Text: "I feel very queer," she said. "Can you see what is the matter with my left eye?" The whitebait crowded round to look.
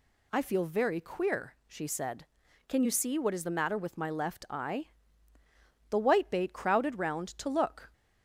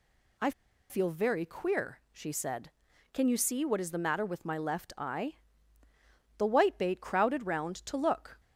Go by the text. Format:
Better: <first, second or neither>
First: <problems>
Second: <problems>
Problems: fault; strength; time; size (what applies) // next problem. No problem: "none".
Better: first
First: none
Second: pauses between "I" and "feel"; at 0.5 s; 0.38 s long